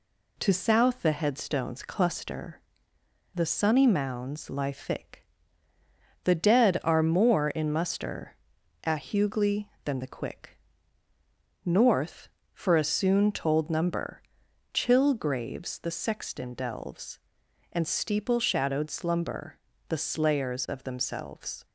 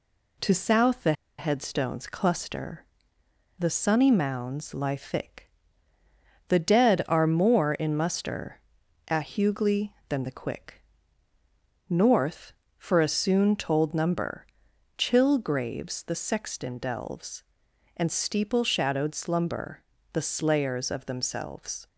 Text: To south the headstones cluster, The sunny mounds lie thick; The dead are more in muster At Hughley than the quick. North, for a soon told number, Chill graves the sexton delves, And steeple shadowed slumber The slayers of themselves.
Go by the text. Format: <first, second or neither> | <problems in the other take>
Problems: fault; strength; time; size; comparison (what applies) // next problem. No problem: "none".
first | pauses between "the" and "headstones"; slight; at 1.1 s; 0.25 s long // pauses between "slumber" and "The"; slight; at 19.8 s; 0.30 s long; slight in the first